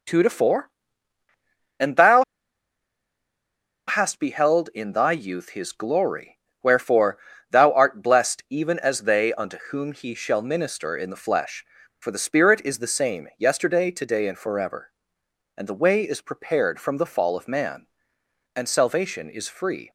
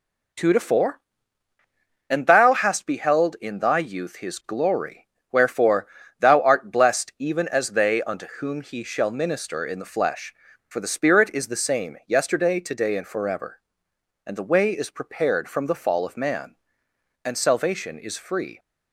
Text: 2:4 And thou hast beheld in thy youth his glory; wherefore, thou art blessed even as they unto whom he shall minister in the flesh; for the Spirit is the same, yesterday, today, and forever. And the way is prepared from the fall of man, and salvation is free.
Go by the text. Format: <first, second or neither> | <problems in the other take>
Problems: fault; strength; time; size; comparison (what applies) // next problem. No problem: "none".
second | pauses between "thou" and "hast"; strong; at 2.2 s; 1.6 s long